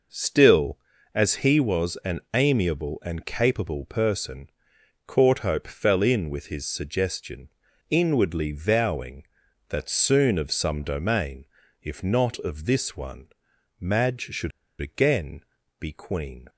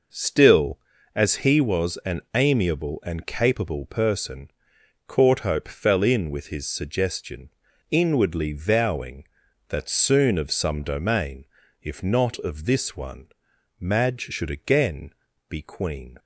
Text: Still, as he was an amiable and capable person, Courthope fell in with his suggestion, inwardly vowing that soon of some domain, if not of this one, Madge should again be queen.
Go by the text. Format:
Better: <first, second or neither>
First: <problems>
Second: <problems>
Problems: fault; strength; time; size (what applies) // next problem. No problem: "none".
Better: second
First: pauses between "an" and "amiable"; slight; at 2.1 s; 0.16 s long // pauses between "should" and "again"; slight; at 14.5 s; 0.30 s long // pauses between "again" and "be"; at 15.4 s; 0.38 s long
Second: pauses between "an" and "amiable"; slight; at 2.1 s; 0.16 s long // pauses between "again" and "be"; at 15.1 s; 0.38 s long